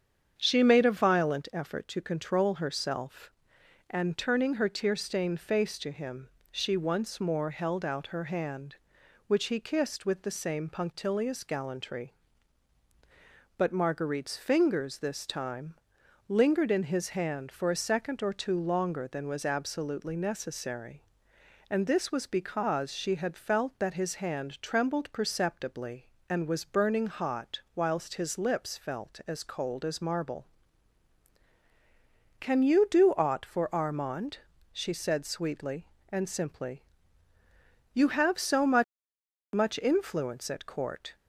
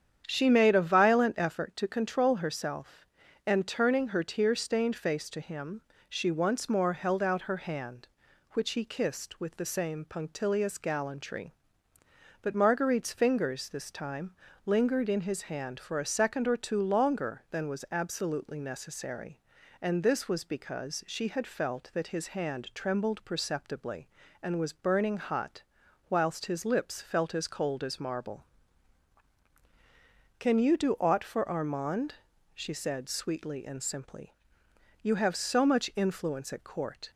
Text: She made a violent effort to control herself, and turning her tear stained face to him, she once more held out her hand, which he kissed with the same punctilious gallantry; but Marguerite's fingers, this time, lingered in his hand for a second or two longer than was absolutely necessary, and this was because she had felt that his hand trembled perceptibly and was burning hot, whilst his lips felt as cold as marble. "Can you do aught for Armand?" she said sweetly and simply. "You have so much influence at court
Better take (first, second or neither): second